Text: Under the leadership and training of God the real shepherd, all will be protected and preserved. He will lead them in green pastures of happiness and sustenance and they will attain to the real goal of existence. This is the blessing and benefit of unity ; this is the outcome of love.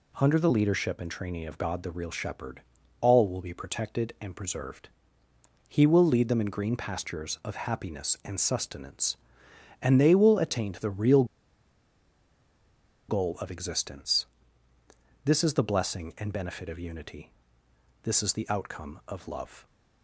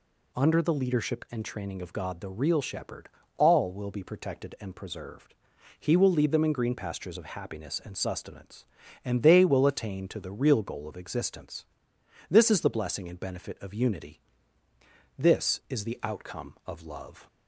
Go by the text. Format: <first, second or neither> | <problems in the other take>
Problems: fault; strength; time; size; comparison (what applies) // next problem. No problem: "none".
second | pauses between "real" and "goal"; strong; at 11.2 s; 1.8 s long